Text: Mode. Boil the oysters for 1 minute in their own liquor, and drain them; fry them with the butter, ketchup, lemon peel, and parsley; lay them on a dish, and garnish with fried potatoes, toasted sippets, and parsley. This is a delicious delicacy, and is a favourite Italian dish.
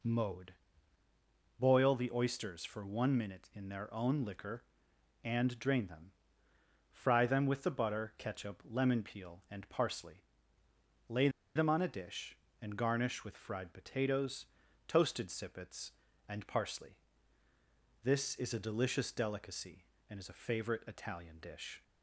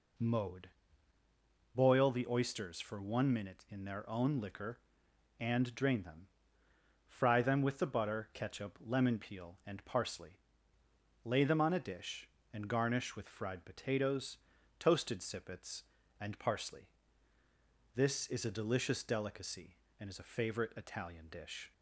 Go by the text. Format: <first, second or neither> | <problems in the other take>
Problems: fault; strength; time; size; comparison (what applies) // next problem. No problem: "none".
second | pauses between "lay" and "them"; slight; at 11.2 s; 0.26 s long